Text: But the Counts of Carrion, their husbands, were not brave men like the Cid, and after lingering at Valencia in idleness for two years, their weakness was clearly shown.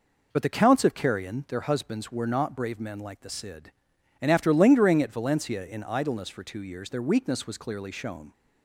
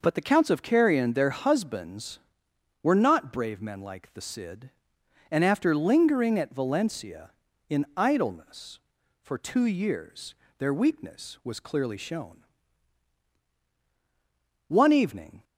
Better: first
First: none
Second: goes on to say "One evening"; noticeable; from 14.6 s on; 0.76 s long

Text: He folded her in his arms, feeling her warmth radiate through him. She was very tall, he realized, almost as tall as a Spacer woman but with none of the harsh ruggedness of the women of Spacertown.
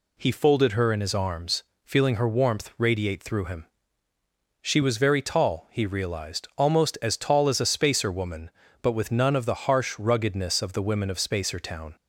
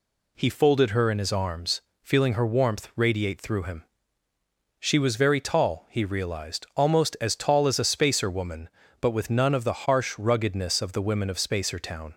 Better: neither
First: none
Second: none

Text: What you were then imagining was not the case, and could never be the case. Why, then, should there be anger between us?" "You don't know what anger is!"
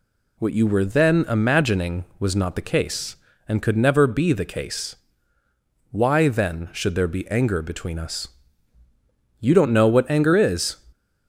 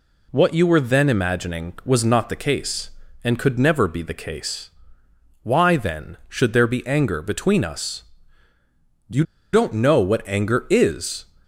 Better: first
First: none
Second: pauses between "You" and "don't"; slight; at 9.2 s; 0.29 s long

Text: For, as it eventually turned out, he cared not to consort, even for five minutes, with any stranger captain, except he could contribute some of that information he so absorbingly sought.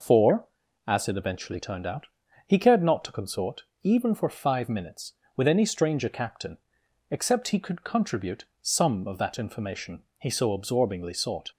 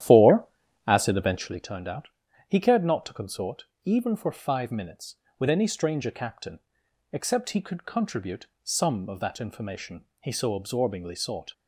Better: first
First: pauses between "contribute" and "some"; slight; at 8.4 s; 0.16 s long // pauses between "information" and "he"; slight; at 10.0 s; 0.16 s long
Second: starts louder than the rest; strong; until 1.5 s; 11.5 dB // pauses between "contribute" and "some"; slight; at 8.4 s; 0.16 s long // pauses between "information" and "he"; slight; at 10.0 s; 0.16 s long

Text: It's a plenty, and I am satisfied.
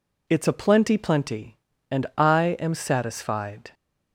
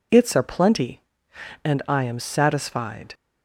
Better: second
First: says "plenty" twice; at 0.9 s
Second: none

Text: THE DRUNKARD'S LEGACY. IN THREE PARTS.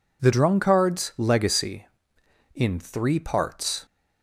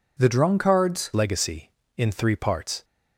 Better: first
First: none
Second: changes voice at "LEGACY"; from 1.1 s on; 1.7 s long

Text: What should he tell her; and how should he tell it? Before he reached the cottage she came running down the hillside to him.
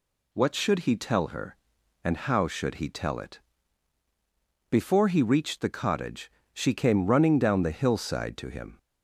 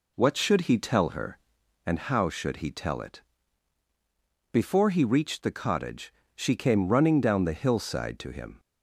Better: first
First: pauses between "cottage" and "she"; slight; at 6.3 s; 0.22 s long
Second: starts louder than the rest; until 1.6 s; 3.5 dB // pauses between "cottage" and "she"; slight; at 6.1 s; 0.22 s long

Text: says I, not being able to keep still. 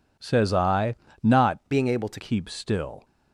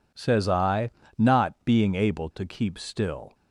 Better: second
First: changes voice from "being" to "to"; from 1.7 to 2.1 s; 0.4 s long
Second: none

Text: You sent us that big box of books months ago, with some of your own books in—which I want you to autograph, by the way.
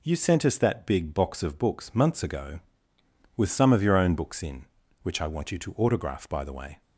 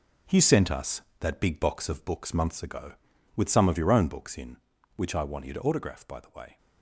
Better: first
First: none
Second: gets quieter; strong; throughout; 8 dB

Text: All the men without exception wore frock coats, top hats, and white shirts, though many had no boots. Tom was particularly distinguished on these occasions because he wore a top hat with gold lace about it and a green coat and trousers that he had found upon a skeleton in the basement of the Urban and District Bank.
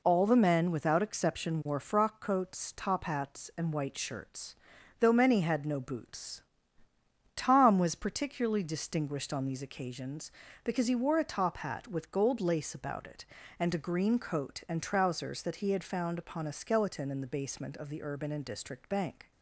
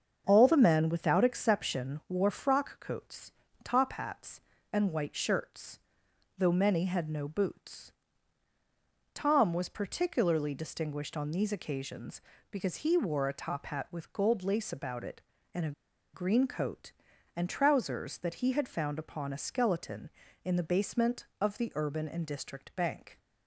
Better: first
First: none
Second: starts louder than the rest; until 1.2 s; 7 dB // pauses between "a" and "green"; at 15.7 s; 0.42 s long

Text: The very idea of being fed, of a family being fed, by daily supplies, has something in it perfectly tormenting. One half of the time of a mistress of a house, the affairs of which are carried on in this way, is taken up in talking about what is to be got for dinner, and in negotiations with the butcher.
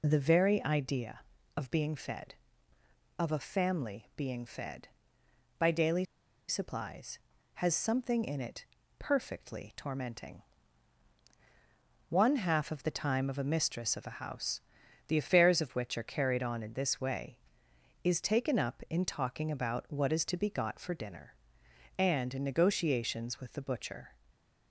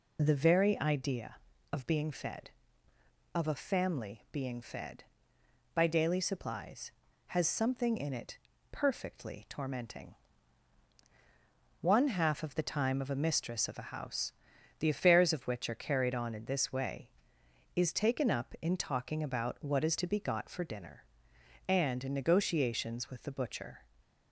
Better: second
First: pauses between "daily" and "supplies"; at 6.0 s; 0.43 s long // pauses between "it" and "perfectly"; slight; at 8.6 s; 0.34 s long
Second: pauses between "it" and "perfectly"; slight; at 8.3 s; 0.34 s long

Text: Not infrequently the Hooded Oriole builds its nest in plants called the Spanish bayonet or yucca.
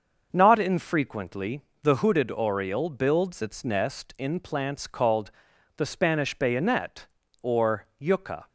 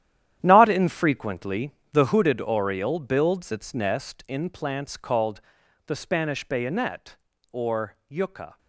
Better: first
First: starts louder than the rest; until 1.3 s; 6 dB // pauses between "infrequently" and "the"; slight; at 1.6 s; 0.22 s long // pauses between "called" and "the"; noticeable; at 5.2 s; 0.46 s long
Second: gets quieter; strong; throughout; 12.5 dB // starts louder than the rest; strong; until 1.4 s; 11 dB // pauses between "infrequently" and "the"; slight; at 1.7 s; 0.22 s long // pauses between "called" and "the"; noticeable; at 5.3 s; 0.46 s long

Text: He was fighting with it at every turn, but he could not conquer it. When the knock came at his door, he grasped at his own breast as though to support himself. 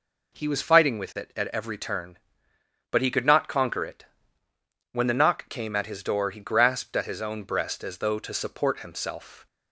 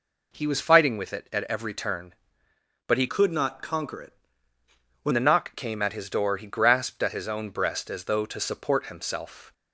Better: first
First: none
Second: changes voice from "could" to "When"; from 3.0 to 5.1 s; 2.1 s long

